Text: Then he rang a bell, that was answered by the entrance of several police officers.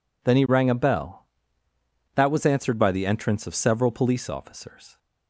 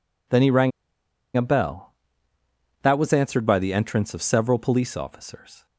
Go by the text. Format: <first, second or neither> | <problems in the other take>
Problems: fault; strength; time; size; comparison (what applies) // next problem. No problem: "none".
first | pauses between "rang" and "a"; noticeable; at 0.7 s; 0.66 s long